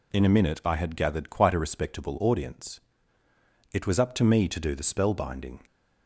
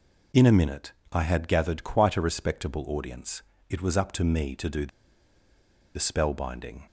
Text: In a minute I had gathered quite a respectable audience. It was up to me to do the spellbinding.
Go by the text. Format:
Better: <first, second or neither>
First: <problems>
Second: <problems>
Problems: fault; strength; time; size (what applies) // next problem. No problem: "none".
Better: first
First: none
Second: pauses between "minute" and "I"; slight; at 0.9 s; 0.18 s long // pauses between "the" and "spellbinding"; at 4.8 s; 1.0 s long